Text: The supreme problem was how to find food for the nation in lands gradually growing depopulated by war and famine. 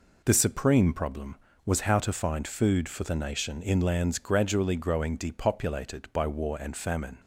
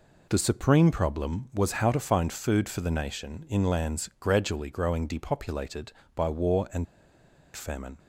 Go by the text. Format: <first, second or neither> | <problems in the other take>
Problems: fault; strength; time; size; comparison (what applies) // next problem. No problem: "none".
first | pauses between "and" and "famine"; noticeable; at 6.8 s; 0.68 s long